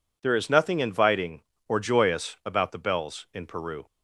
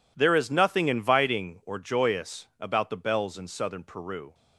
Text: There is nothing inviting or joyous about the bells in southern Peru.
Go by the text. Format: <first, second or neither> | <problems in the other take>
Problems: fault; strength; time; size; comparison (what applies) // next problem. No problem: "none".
second | skips "southern"; at 3.4 s